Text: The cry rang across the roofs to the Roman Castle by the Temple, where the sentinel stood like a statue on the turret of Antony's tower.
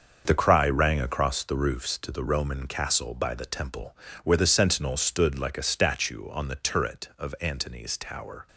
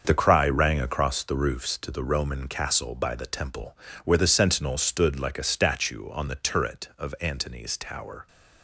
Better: neither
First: starts louder than the rest; until 1.2 s; 6.5 dB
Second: starts louder than the rest; until 1.0 s; 6.5 dB

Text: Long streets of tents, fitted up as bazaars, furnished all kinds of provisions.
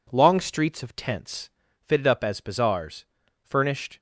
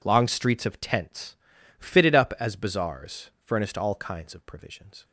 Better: second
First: stops before "all kinds of provisions"; at 3.9 s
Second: none

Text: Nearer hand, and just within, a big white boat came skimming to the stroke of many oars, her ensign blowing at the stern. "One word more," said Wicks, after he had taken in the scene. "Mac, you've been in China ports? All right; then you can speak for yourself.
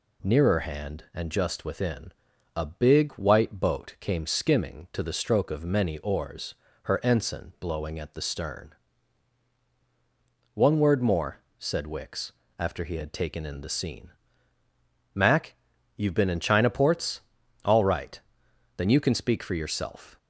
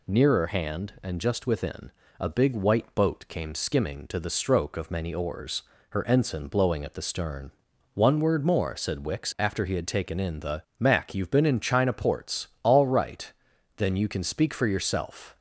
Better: first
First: none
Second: skips "scene"; at 10.7 s

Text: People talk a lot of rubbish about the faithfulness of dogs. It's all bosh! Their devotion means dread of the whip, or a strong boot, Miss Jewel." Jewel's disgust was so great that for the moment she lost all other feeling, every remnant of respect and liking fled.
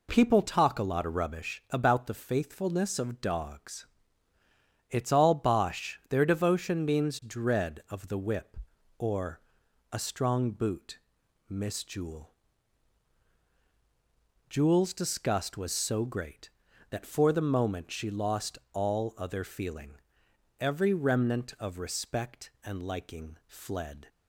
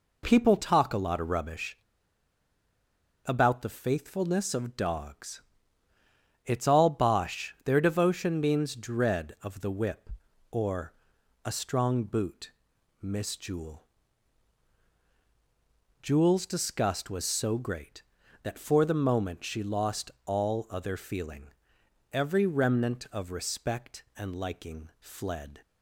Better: first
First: pauses between "or" and "a"; noticeable; at 9.4 s; 0.50 s long // pauses between "lost" and "all"; slight; at 18.5 s; 0.16 s long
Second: pauses between "rubbish" and "about"; strong; at 1.7 s; 1.4 s long // pauses between "or" and "a"; noticeable; at 10.9 s; 0.50 s long // pauses between "lost" and "all"; slight; at 20.1 s; 0.16 s long

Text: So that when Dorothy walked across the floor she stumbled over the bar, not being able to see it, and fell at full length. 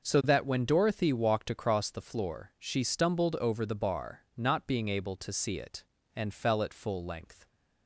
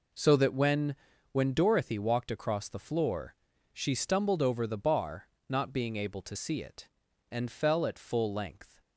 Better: first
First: none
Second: says "when" twice; at 1.3 s // pauses between "floor" and "she"; at 3.3 s; 0.38 s long

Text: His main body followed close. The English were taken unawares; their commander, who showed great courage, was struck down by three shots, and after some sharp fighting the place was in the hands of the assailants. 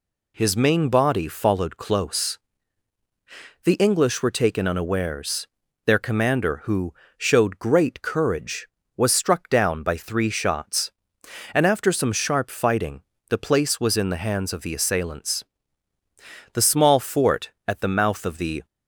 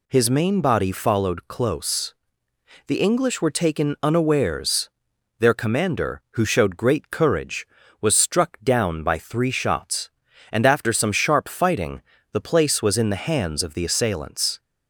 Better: second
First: pauses between "who" and "showed"; slight; at 6.9 s; 0.24 s long // pauses between "fighting" and "the"; slight; at 12.9 s; 0.30 s long // goes on to say "The small fort at the mouth of the"; strong; from 16.5 s on; 2.1 s long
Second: pauses between "fighting" and "the"; slight; at 12.0 s; 0.32 s long

